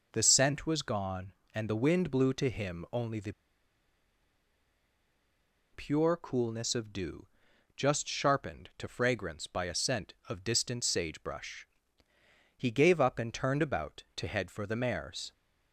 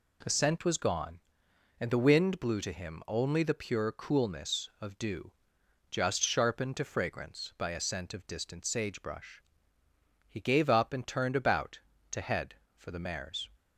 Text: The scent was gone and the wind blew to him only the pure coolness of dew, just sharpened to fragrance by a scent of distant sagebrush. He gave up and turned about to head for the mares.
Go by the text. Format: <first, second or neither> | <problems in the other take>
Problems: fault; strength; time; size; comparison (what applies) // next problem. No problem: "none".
second | pauses between "the" and "pure"; strong; at 3.3 s; 2.4 s long